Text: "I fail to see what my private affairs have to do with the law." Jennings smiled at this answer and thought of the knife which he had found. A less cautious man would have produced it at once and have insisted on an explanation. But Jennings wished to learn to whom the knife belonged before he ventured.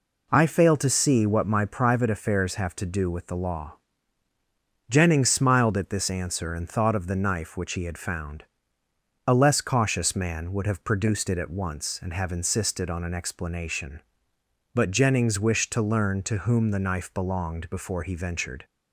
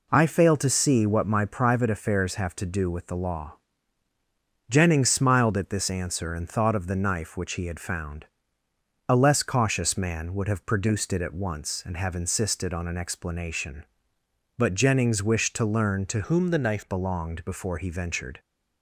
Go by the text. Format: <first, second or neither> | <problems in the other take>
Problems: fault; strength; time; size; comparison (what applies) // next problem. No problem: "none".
first | changes voice from "whom" to "knife"; from 16.2 to 16.8 s; 0.6 s long